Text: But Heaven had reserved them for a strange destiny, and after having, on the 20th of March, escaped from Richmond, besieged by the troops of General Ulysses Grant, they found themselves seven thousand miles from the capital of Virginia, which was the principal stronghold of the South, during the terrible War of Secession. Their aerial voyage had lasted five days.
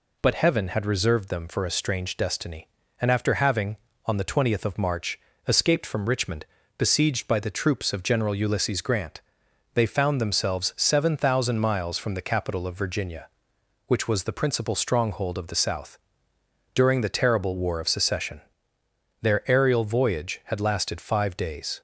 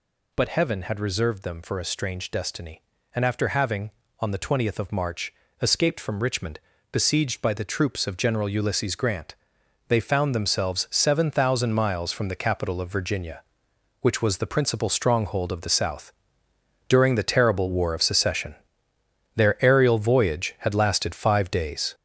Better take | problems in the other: first | gets louder; throughout; 6.5 dB

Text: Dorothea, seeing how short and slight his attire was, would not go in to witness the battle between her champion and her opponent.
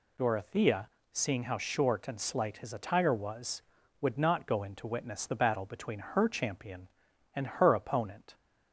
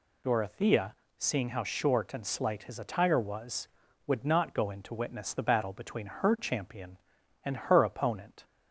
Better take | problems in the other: neither | none

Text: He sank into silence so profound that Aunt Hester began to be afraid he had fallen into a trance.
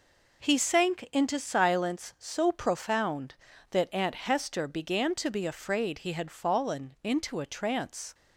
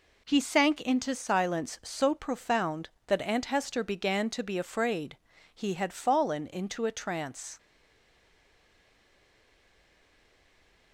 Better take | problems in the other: first | pauses between "afraid" and "he"; slight; at 5.1 s; 0.34 s long // stays silent after the last word; strong; from 7.5 s on; 3.4 s long

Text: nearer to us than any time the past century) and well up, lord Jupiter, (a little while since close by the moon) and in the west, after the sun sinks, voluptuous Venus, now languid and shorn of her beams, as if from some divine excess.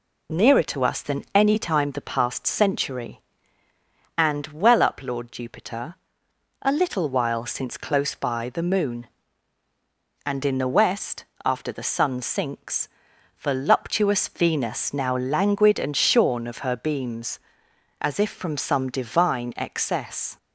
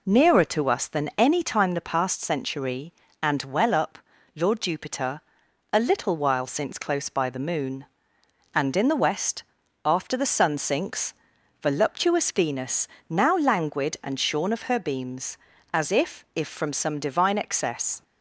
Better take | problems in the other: first | says "if" twice; at 16.3 s

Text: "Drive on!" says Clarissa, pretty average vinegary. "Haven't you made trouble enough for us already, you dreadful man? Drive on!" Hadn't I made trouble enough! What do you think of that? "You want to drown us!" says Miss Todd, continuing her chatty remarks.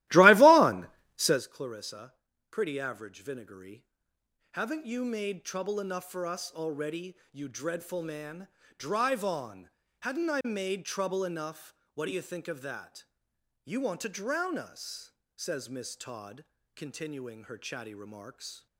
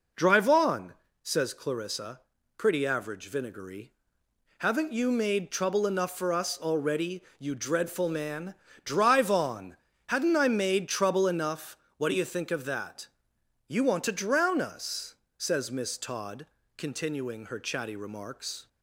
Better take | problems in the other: second | starts louder than the rest; strong; until 1.4 s; 16.5 dB

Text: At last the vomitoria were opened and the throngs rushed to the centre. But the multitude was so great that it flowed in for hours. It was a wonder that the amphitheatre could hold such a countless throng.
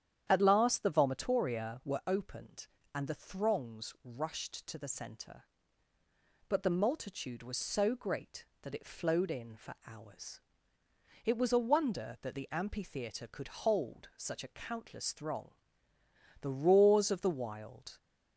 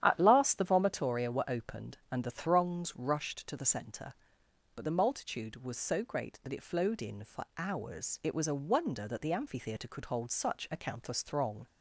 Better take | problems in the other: second | starts louder than the rest; strong; until 1.3 s; 9.5 dB; strong in the second // goes on to say "The roars of the wild"; from 16.4 s on; 1.5 s long

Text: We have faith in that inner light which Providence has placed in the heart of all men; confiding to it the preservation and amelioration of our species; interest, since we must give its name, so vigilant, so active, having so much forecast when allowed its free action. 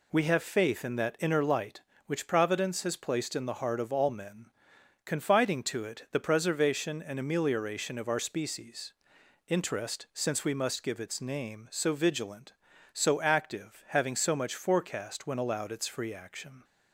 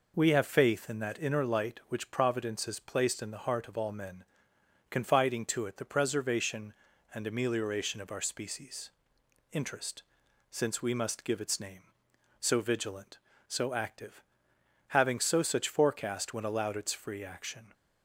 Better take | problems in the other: first | says "such" for "much"; at 15.4 s

